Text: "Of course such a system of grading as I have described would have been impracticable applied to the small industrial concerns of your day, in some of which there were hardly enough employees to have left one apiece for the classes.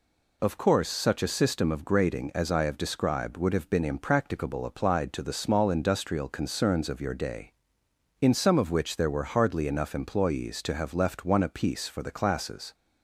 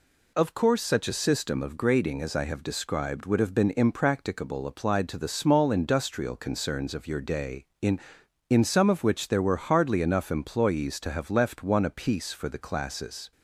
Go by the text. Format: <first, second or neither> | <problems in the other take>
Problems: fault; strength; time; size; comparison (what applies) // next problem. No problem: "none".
first | says "in" twice; at 8.4 s